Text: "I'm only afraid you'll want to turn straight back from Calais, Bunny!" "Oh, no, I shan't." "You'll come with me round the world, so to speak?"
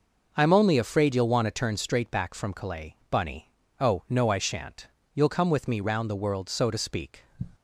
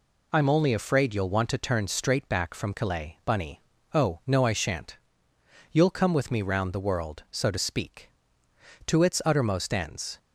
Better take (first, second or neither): first